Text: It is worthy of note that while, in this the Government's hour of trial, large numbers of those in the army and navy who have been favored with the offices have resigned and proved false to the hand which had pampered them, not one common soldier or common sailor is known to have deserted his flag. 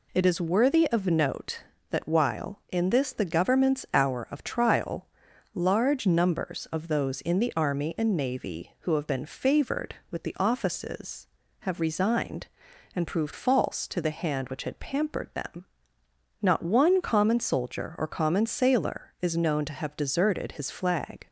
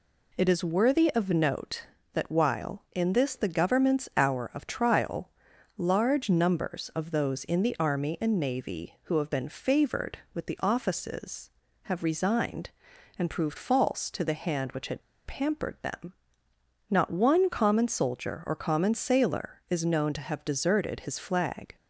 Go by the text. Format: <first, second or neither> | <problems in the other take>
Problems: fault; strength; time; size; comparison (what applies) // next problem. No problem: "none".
first | pauses between "had" and "pampered"; slight; at 15.0 s; 0.23 s long